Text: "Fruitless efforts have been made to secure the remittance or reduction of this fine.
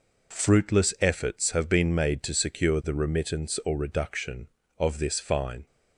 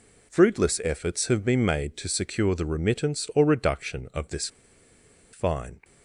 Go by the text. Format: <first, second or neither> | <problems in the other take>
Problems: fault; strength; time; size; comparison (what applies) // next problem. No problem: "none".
first | pauses between "this" and "fine"; noticeable; at 4.4 s; 0.85 s long